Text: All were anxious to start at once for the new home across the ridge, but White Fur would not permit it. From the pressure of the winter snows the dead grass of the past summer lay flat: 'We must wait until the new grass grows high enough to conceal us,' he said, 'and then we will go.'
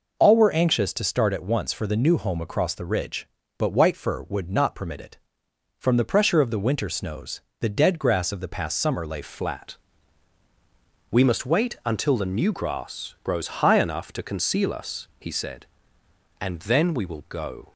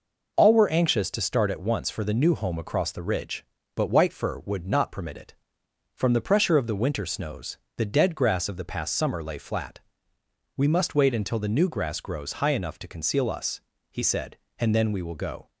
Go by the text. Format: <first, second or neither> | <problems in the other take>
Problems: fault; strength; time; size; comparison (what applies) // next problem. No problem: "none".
second | pauses between "snows" and "the"; slight; at 7.4 s; 0.18 s long; slight in the second // changes voice at "flat"; from 9.2 s on; 8.5 s long